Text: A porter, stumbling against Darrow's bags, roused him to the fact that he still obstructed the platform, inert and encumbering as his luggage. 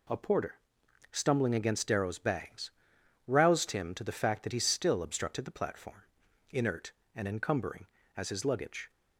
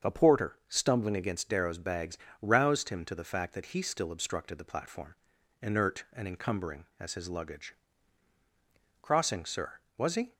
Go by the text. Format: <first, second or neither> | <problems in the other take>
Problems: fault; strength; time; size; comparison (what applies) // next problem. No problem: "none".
first | starts louder than the rest; until 1.1 s; 7 dB // goes on to say "Crossing sir Was he"; from 9.0 s on; 1.3 s long